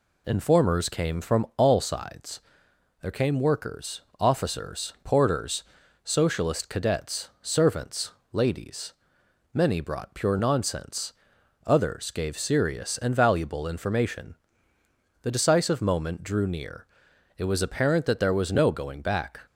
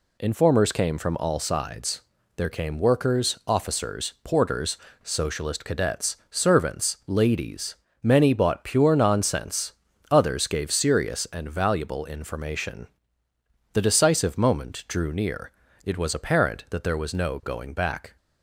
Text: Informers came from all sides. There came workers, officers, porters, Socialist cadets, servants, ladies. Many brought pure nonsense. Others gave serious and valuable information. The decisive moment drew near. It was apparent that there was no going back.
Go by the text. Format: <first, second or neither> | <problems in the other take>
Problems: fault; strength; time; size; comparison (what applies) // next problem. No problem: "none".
first | says "bought" for "brought"; at 8.3 s